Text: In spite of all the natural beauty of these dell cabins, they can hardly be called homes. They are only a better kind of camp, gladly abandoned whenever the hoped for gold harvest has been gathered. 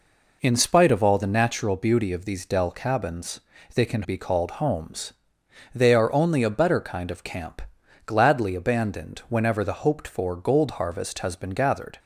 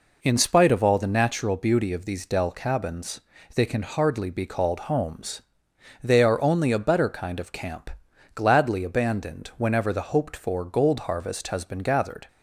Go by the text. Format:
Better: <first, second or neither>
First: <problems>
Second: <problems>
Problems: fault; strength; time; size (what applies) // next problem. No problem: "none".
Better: second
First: skips "hardly"; at 4.0 s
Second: none